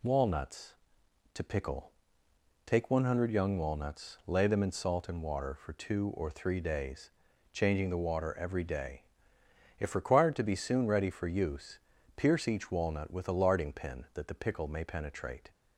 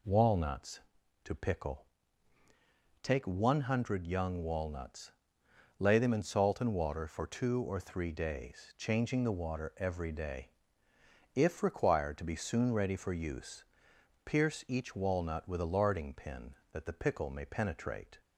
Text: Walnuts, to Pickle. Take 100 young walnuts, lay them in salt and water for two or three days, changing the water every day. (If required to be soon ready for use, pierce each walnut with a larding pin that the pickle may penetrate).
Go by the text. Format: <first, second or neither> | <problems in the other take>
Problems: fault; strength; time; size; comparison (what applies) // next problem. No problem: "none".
neither | none